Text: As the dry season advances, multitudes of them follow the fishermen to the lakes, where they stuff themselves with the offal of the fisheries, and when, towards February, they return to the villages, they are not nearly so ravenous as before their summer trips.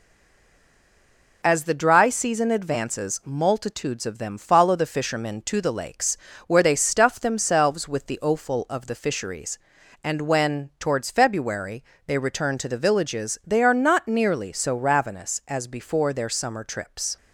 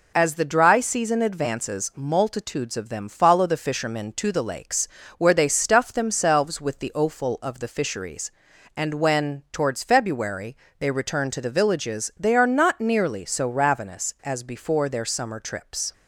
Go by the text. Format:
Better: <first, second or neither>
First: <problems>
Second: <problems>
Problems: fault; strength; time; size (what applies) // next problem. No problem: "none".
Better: second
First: stays silent before the first word; noticeable; until 1.4 s; 1.4 s long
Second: none